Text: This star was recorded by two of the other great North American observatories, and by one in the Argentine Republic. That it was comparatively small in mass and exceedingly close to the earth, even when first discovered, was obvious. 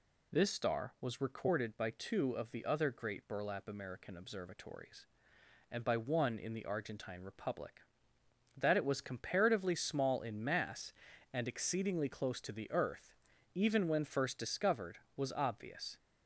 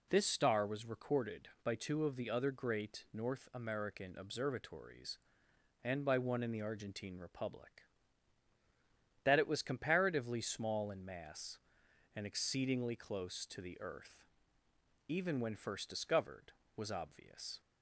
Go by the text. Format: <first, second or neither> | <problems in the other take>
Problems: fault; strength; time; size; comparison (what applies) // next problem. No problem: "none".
second | says "Burlap" for "North"; at 3.2 s